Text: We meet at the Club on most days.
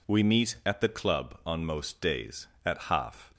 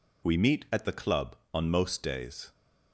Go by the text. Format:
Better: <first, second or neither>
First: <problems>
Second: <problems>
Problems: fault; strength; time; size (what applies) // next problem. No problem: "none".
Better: second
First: goes on to say "At half"; noticeable; from 2.6 s on; 0.68 s long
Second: none